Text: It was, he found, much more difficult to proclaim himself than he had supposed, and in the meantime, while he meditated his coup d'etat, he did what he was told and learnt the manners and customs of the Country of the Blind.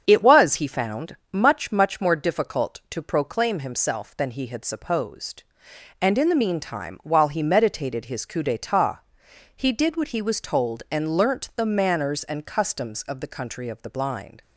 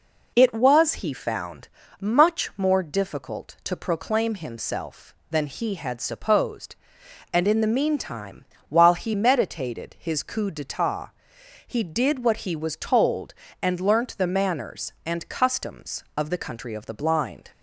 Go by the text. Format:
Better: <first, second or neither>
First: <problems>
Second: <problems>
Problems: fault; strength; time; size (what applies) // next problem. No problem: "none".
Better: second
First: starts louder than the rest; strong; until 1.0 s; 7.5 dB // says "much" twice; at 1.7 s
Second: none